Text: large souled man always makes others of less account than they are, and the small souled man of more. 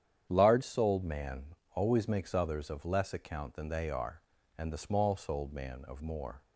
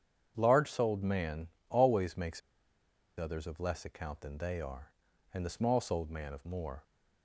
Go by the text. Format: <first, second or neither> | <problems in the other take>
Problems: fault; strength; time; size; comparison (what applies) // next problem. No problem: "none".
first | starts louder than the rest; strong; until 1.3 s; 8 dB; strong in the first // pauses between "man" and "always"; slight; at 1.4 s; 0.22 s long; slight in the first // pauses between "makes" and "others"; noticeable; at 2.4 s; 0.78 s long